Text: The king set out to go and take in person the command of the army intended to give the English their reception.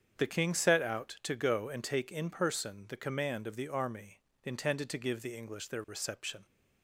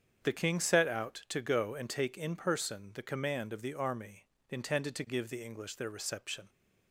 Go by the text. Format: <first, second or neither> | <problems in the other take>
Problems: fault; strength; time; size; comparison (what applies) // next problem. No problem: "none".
neither | starts louder than the rest; strong; the same in both // pauses between "army" and "intended"; slight; the same in both